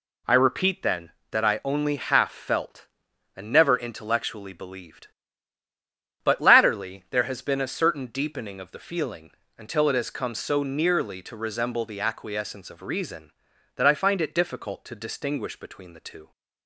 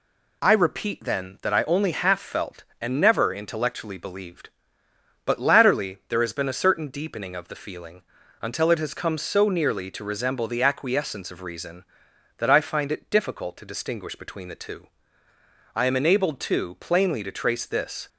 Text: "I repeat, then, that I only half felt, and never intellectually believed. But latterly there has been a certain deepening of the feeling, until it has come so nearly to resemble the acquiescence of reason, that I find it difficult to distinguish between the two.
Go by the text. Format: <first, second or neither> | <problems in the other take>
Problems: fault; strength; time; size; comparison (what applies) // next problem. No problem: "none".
first | goes on to say "I am enabled too plainly to trace this"; strong; from 15.7 s on; 2.3 s long